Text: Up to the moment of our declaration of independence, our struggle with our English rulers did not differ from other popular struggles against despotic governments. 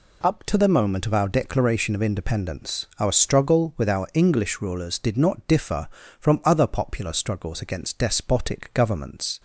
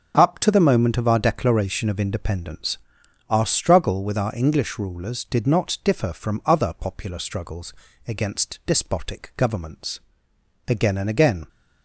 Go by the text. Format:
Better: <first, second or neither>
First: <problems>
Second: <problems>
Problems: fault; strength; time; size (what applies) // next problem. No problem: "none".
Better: first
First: none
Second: starts louder than the rest; noticeable; until 1.1 s; 6 dB // pauses between "struggles" and "against"; slight; at 7.7 s; 0.34 s long // goes on to say "Again and again"; noticeable; from 10.6 s on; 0.82 s long